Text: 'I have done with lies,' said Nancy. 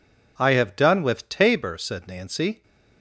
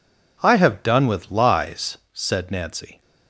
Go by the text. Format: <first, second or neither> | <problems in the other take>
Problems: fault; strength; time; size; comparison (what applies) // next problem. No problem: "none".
second | says "tabor" for "lies"; at 1.2 s